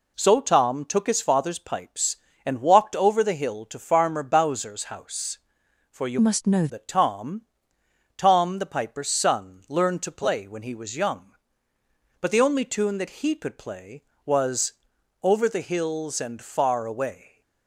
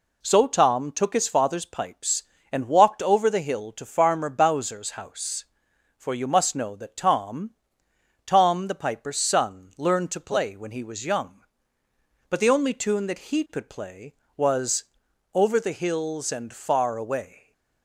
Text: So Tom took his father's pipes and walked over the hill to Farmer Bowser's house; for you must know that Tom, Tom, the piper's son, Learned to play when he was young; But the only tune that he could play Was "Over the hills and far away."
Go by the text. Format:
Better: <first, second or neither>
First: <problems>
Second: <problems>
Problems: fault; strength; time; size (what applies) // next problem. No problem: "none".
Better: second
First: changes voice from "must" to "know"; from 6.1 to 6.6 s; 0.5 s long // pauses between "Was" and "Over"; noticeable; at 14.7 s; 0.50 s long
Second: pauses between "Was" and "Over"; noticeable; at 14.8 s; 0.50 s long